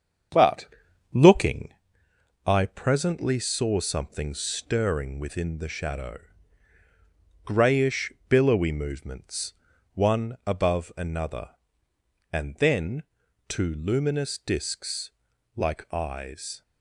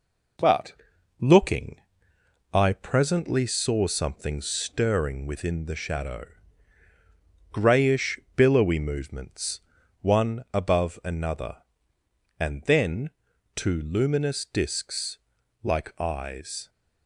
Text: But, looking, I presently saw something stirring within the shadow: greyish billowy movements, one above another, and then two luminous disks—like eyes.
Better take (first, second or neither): second